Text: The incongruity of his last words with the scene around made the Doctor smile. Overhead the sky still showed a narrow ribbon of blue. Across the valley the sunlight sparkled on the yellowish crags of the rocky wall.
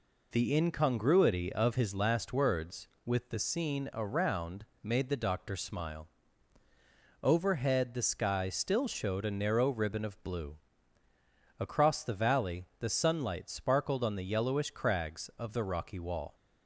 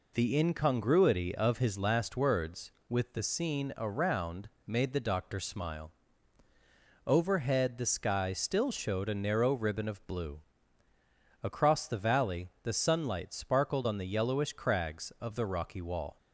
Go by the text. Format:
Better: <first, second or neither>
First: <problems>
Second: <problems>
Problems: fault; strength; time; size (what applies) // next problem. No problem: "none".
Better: neither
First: pauses between "around" and "made"; slight; at 4.6 s; 0.16 s long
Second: pauses between "around" and "made"; slight; at 4.4 s; 0.16 s long